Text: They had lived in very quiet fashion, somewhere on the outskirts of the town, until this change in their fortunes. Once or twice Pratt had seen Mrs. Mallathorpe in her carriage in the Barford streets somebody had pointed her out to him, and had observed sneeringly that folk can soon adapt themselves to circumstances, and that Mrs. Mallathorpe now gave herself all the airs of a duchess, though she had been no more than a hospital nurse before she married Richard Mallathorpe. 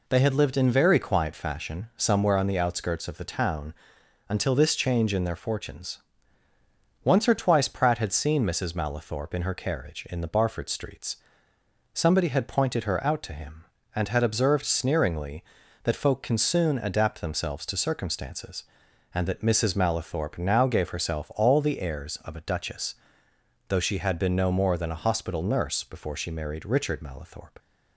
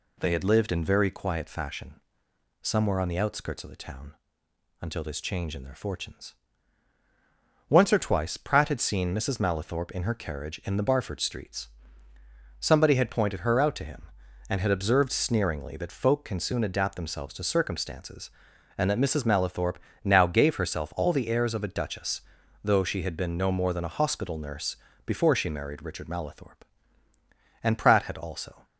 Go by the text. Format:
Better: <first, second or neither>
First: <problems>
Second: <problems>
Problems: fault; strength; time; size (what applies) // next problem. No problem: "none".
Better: first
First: pauses between "streets" and "somebody"; noticeable; at 11.1 s; 0.76 s long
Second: pauses between "streets" and "somebody"; noticeable; at 11.6 s; 0.92 s long // pauses between "Mallathorpe" and "now"; slight; at 19.7 s; 0.26 s long // pauses between "nurse" and "before"; slight; at 24.7 s; 0.30 s long // goes on to say "And Pratt had also"; noticeable; from 27.6 s on; 1.0 s long